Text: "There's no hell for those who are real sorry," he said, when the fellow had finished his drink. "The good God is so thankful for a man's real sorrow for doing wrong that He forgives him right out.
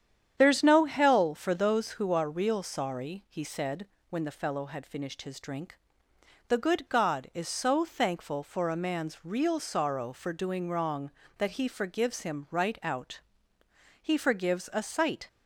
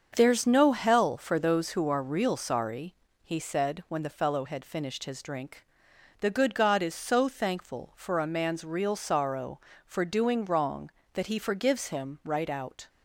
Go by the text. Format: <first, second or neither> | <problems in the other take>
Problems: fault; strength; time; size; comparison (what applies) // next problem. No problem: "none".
second | starts louder than the rest; strong; until 1.3 s; 9 dB; also in the second // goes on to say "He forgives a sight"; noticeable; from 14.0 s on; 1.2 s long